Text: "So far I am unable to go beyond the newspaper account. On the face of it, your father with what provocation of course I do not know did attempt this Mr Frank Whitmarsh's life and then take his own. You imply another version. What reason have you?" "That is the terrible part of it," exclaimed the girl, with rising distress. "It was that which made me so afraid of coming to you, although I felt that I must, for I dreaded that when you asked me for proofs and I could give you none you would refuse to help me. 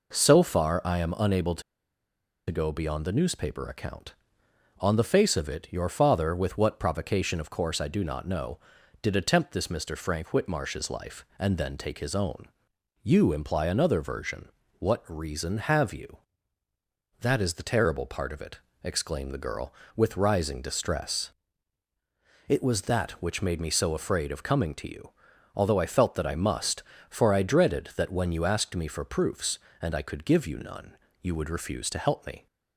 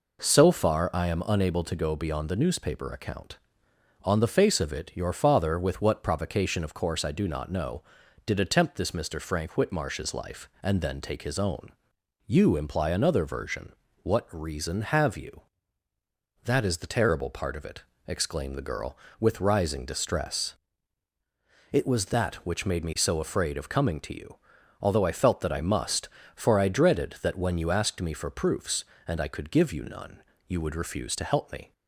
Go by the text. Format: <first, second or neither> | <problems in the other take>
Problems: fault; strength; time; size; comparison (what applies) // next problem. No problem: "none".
second | pauses between "to" and "go"; noticeable; at 1.6 s; 0.87 s long // pauses between "none" and "you"; slight; at 30.9 s; 0.26 s long; slight in the second